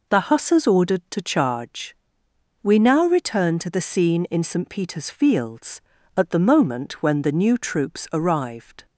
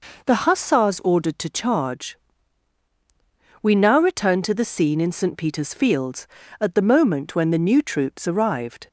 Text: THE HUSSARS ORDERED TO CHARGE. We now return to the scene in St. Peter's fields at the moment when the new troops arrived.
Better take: neither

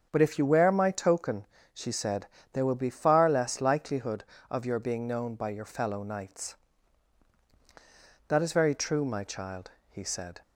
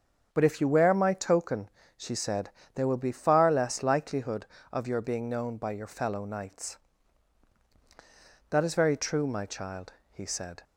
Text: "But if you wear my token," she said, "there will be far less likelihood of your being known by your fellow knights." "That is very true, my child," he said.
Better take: neither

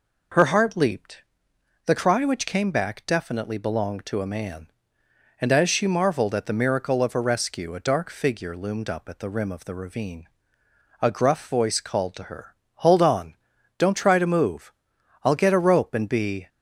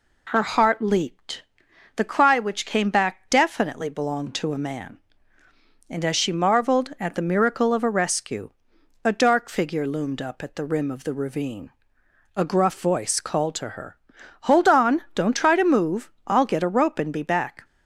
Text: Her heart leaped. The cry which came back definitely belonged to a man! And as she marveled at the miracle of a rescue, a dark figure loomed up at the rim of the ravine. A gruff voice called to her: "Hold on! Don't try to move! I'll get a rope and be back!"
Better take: second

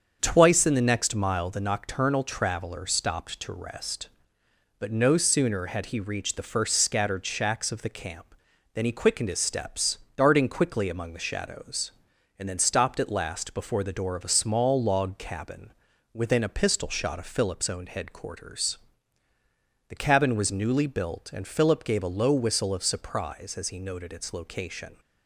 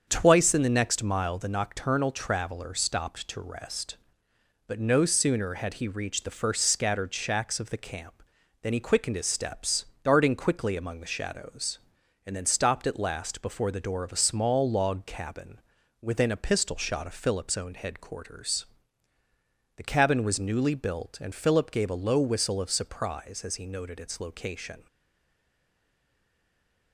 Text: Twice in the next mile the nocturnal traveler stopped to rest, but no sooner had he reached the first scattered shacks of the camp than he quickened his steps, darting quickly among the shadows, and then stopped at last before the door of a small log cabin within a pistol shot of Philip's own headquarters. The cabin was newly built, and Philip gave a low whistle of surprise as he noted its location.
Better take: first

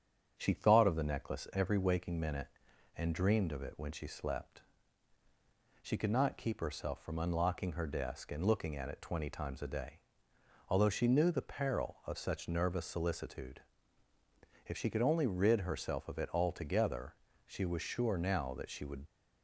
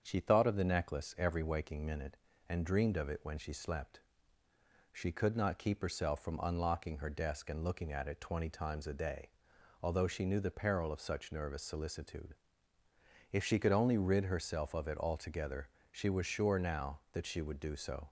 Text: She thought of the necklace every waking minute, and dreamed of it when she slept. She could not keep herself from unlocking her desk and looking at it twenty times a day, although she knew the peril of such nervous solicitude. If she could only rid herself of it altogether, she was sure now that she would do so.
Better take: second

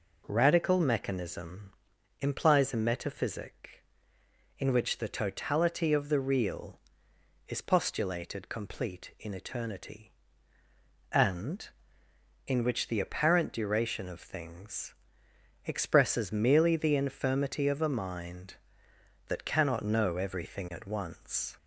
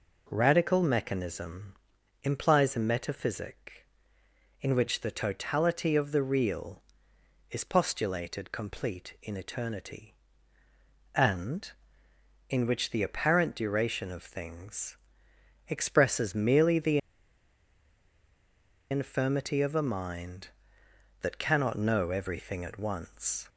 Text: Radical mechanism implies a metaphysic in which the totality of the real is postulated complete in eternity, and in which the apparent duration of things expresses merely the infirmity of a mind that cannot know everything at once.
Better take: first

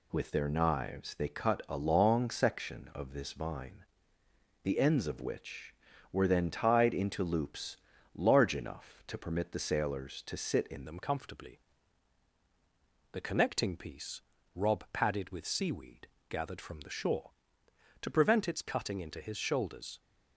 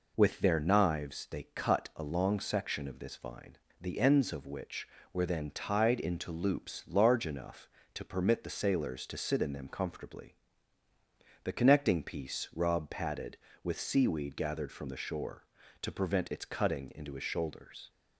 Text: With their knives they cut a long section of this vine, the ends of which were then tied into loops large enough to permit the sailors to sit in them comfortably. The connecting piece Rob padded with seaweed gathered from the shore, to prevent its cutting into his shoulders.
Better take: second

